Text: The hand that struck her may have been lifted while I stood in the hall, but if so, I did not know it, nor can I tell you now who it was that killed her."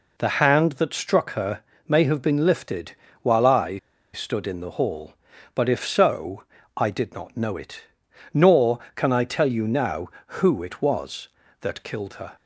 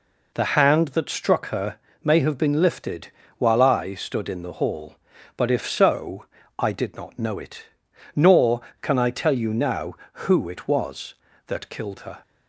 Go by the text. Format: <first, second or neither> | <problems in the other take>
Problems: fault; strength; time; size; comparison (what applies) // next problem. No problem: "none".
second | pauses between "her" and "may"; slight; at 1.6 s; 0.26 s long; slight in the second // pauses between "lifted" and "while"; slight; at 2.9 s; 0.28 s long; slight in the second // pauses between "I" and "stood"; at 3.7 s; 0.36 s long